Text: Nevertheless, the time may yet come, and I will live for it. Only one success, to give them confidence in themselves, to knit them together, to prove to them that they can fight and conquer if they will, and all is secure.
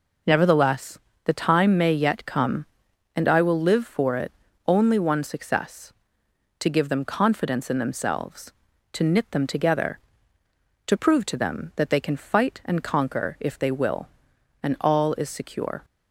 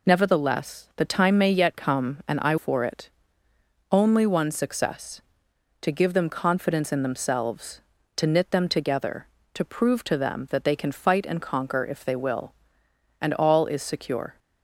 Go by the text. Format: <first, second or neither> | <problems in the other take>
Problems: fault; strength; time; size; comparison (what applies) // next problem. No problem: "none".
first | skips "will live"; at 2.5 s